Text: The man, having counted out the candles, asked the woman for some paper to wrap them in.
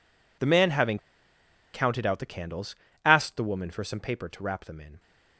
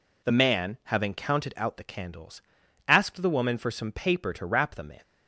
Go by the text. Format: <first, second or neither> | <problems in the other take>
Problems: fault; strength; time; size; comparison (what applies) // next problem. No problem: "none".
second | pauses between "having" and "counted"; noticeable; at 0.9 s; 0.75 s long